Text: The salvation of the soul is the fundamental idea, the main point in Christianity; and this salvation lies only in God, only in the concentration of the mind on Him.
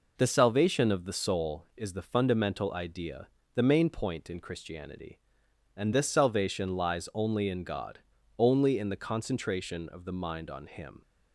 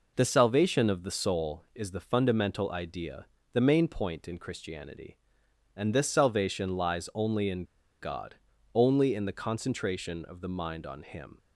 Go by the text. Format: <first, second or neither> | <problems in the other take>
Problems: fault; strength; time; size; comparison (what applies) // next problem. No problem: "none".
first | pauses between "in" and "God"; at 7.6 s; 0.38 s long